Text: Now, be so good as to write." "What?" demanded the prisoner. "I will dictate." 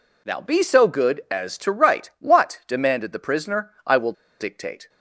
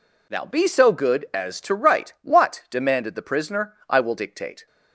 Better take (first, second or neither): second